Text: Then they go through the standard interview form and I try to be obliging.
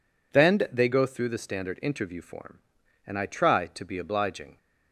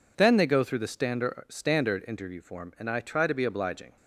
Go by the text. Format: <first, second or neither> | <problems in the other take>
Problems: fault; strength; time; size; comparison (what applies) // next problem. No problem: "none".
first | says "standard" twice; at 1.4 s